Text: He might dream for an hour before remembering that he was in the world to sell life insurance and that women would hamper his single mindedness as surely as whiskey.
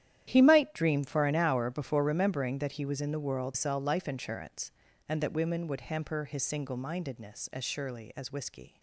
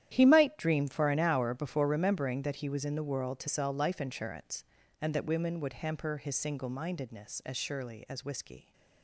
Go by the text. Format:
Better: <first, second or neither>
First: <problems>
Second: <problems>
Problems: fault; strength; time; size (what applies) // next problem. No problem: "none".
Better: second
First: starts louder than the rest; strong; until 1.3 s; 11 dB // skips "to"; at 3.5 s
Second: starts louder than the rest; strong; until 1.1 s; 11 dB